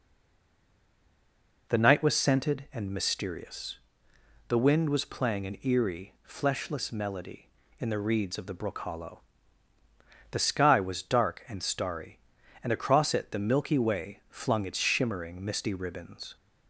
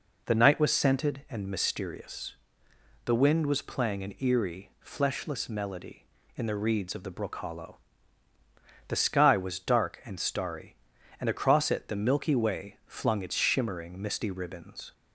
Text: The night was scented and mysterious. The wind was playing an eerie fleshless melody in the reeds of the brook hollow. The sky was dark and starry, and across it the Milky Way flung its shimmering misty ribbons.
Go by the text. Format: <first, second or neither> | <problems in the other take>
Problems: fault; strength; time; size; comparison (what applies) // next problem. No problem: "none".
second | stays silent before the first word; noticeable; until 1.6 s; 1.6 s long